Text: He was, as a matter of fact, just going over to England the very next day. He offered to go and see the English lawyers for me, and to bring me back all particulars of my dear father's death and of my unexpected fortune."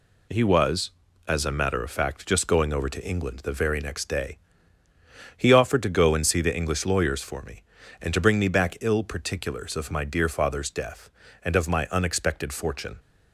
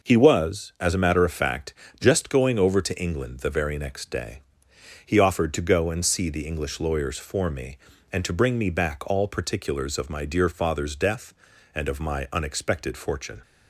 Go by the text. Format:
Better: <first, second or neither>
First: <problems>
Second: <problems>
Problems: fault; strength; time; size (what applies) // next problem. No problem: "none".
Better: second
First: says "ill" for "all"; at 8.7 s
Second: none